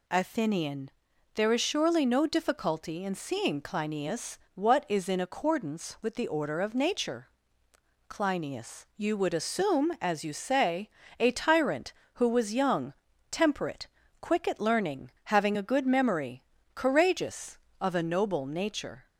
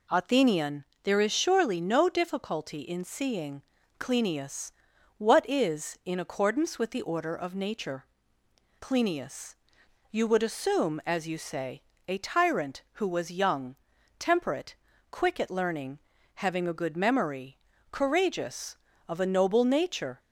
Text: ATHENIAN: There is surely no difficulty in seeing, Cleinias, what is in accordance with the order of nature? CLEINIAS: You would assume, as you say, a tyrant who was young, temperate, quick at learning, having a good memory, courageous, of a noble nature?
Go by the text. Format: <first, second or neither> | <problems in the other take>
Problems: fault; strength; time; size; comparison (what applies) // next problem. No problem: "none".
neither | none